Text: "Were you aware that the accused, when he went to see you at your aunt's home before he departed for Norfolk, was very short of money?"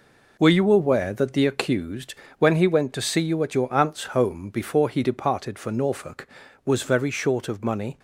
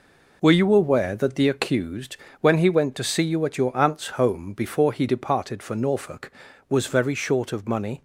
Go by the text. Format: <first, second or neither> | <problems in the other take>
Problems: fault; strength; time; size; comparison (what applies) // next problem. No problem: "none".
neither | none